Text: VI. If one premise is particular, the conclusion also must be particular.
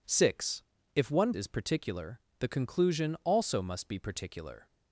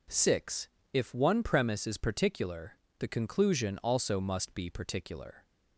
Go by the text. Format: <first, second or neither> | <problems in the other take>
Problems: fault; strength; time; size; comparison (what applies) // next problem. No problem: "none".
second | skips "premise"; at 1.3 s